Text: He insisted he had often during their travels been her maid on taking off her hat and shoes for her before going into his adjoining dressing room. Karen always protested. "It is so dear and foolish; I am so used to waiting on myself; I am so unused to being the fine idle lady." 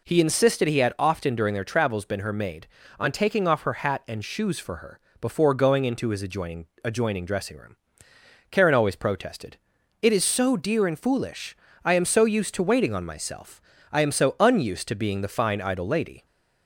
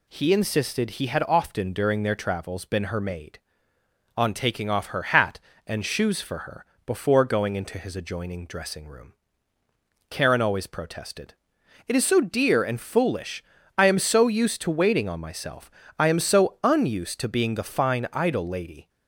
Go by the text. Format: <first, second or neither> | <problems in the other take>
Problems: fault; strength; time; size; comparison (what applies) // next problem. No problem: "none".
second | pauses between "her" and "before"; slight; at 4.9 s; 0.22 s long; slight in the second // says "adjoining" twice; at 6.8 s